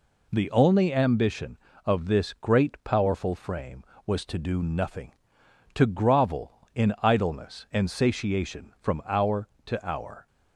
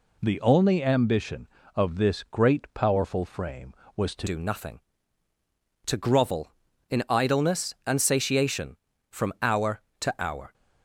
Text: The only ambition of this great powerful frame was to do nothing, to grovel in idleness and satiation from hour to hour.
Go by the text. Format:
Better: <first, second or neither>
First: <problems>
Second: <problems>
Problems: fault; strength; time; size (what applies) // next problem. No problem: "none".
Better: first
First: none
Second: changes voice at "do"; from 4.2 s on; 6.3 s long